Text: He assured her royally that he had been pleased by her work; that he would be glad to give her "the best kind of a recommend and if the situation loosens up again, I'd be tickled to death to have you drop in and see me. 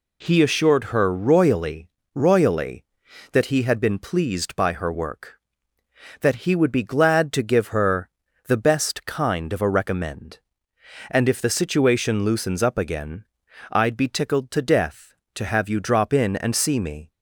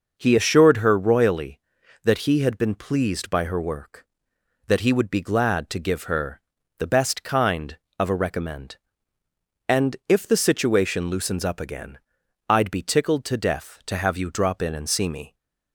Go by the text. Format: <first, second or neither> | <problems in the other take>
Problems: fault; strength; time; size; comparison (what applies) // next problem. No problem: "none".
second | says "royally" twice; at 2.1 s // pauses between "her" and "the"; slight; at 8.1 s; 0.34 s long; also in the second